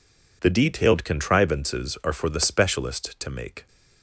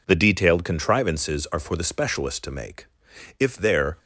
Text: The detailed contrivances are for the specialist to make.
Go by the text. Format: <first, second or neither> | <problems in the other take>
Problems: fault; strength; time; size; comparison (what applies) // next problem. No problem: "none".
first | goes on to say "If there"; from 3.3 s on; 0.58 s long